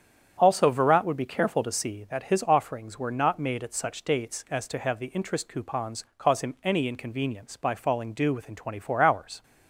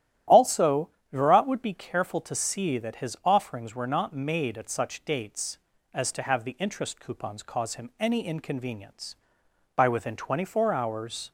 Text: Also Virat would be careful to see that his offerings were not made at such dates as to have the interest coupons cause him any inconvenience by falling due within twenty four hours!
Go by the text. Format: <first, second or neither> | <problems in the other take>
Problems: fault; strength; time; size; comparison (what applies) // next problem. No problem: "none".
first | starts louder than the rest; strong; until 1.5 s; 12 dB; strong in the first // pauses between "Also" and "Virat"; slight; at 0.8 s; 0.22 s long // skips "falling due"; at 9.8 s